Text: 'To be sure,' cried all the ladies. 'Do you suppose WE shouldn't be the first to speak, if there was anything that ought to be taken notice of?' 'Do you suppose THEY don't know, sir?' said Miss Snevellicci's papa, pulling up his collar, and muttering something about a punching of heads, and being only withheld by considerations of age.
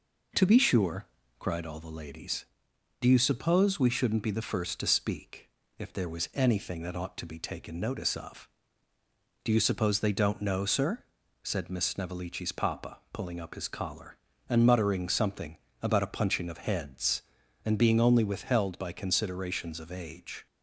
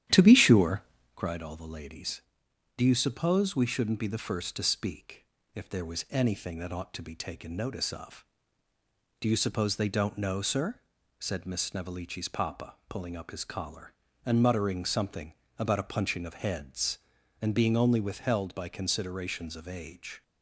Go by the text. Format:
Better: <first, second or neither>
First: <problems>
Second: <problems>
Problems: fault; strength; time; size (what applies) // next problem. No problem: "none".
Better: first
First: pauses between "something" and "about"; slight; at 15.5 s; 0.26 s long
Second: starts louder than the rest; strong; until 1.1 s; 11 dB // pauses between "something" and "about"; slight; at 15.3 s; 0.26 s long